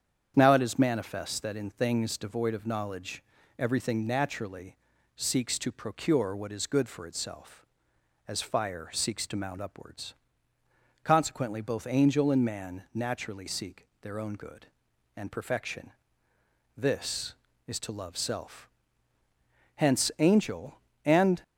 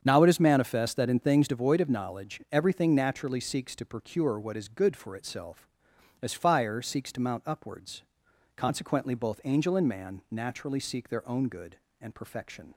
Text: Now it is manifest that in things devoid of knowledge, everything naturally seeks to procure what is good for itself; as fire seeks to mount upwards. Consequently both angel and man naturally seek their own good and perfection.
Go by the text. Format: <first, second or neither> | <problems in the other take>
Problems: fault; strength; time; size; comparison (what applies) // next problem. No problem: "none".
second | starts louder than the rest; strong; until 1.3 s; 8 dB; strong in the second // pauses between "naturally" and "seeks"; at 4.7 s; 0.40 s long // pauses between "seek" and "their"; slight; at 13.8 s; 0.16 s long // goes on to say "This is to love self Hence angel and"; strong; from 16.7 s on; 4.6 s long